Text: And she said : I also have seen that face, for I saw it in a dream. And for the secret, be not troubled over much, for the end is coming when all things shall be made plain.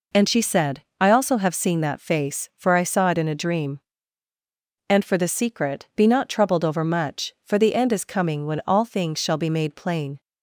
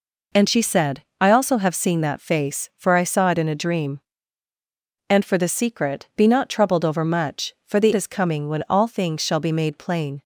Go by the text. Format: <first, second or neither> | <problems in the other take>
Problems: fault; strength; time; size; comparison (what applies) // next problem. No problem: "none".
first | skips "end"; at 7.9 s